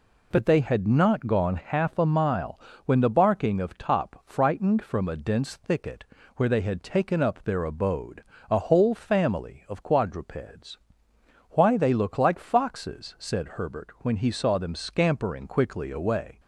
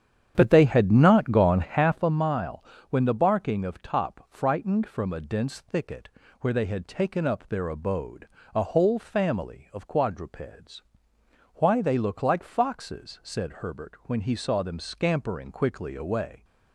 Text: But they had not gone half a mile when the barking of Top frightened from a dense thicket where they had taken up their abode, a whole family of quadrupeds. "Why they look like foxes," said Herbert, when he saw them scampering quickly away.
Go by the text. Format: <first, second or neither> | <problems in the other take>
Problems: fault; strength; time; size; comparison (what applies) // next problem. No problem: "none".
first | starts louder than the rest; strong; until 2.2 s; 9 dB // pauses between "mile" and "when"; slight; at 2.6 s; 0.28 s long; slight in the first // pauses between "thicket" and "where"; slight; at 6.0 s; 0.32 s long; slight in the first